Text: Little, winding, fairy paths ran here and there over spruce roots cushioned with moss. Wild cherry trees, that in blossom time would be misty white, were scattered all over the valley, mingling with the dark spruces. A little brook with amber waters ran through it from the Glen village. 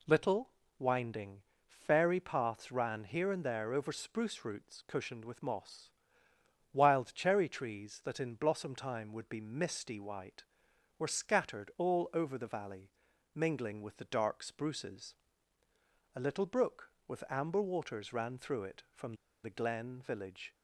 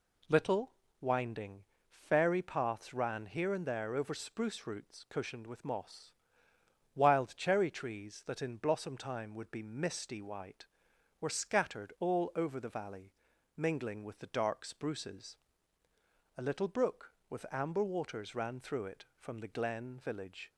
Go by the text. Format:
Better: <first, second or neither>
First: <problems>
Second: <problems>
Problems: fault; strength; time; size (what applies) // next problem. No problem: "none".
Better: second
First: pauses between "from" and "the"; slight; at 19.1 s; 0.29 s long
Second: none